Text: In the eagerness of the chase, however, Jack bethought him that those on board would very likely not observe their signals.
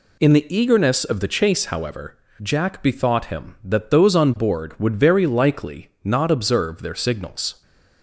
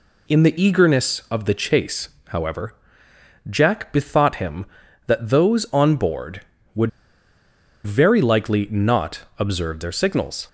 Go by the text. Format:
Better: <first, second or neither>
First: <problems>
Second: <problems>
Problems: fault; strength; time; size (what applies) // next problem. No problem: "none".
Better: first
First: none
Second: pauses between "would" and "very"; noticeable; at 6.8 s; 0.95 s long // pauses between "not" and "observe"; slight; at 9.2 s; 0.16 s long